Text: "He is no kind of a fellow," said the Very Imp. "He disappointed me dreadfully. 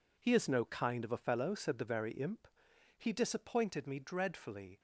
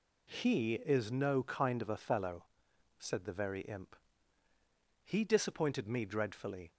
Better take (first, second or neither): neither